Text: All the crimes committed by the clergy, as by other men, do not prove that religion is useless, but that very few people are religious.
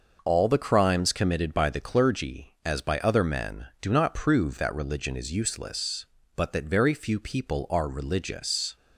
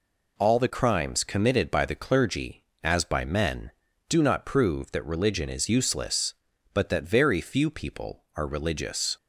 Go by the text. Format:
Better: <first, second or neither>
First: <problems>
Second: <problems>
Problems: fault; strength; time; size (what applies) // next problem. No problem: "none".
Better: first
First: none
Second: skips "other"; at 3.2 s